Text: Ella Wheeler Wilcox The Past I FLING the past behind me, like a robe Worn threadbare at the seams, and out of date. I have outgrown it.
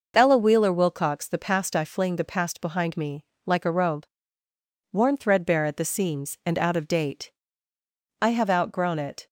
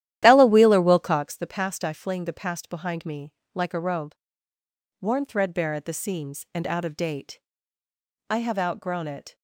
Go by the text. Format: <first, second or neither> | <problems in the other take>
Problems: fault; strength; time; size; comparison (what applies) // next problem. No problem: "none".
first | starts louder than the rest; strong; until 1.4 s; 12.5 dB // pauses between "robe" and "Worn"; noticeable; at 4.1 s; 0.88 s long; noticeable in the first